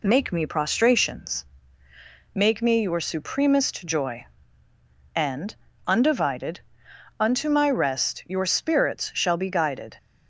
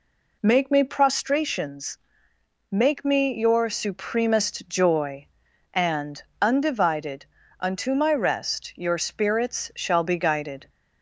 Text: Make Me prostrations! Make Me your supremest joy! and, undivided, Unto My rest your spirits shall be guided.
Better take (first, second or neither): neither